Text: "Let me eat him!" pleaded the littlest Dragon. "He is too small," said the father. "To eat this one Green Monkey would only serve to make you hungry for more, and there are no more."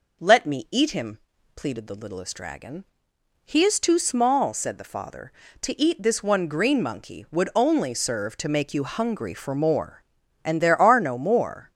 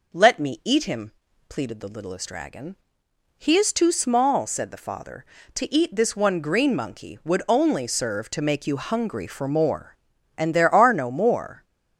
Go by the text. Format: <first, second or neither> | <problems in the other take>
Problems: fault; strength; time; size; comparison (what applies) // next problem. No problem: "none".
neither | none